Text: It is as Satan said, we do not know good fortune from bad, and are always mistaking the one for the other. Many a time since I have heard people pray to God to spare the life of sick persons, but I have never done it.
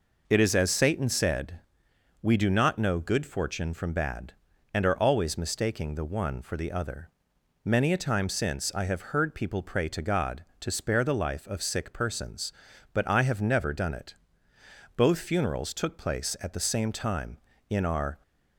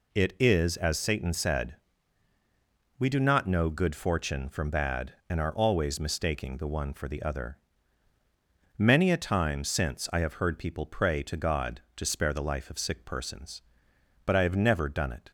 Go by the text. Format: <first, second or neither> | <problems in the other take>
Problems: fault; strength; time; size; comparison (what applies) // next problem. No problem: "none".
second | goes on to say "Both funerals took place at the same time in our"; strong; from 14.9 s on; 3.2 s long